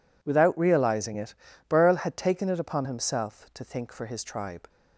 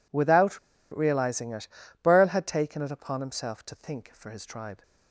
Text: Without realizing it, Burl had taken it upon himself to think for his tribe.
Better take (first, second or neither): first